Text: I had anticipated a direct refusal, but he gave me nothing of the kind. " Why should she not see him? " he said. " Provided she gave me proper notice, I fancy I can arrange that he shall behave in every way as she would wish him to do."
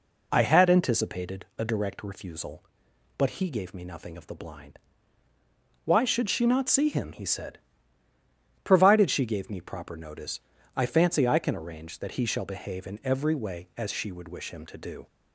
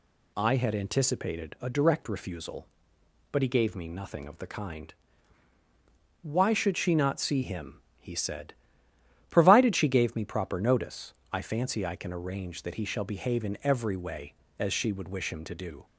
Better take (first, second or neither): second